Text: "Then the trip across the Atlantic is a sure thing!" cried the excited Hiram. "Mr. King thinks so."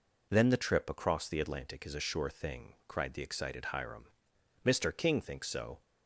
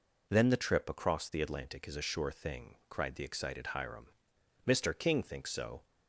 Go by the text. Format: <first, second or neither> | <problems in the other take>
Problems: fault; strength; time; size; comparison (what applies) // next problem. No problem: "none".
neither | none